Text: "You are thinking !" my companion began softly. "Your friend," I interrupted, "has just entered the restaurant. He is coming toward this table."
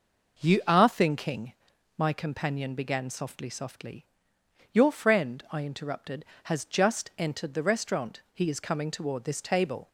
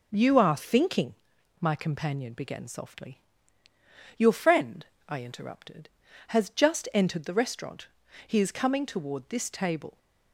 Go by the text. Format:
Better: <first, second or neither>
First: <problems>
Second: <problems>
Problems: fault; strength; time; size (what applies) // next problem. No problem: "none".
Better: second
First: says "softly" twice; at 3.4 s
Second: none